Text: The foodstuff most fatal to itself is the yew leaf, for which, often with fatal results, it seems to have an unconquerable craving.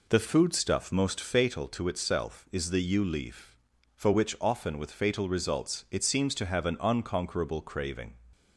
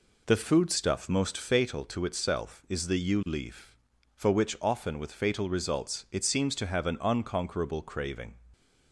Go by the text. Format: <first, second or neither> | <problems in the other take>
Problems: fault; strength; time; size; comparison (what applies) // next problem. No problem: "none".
neither | none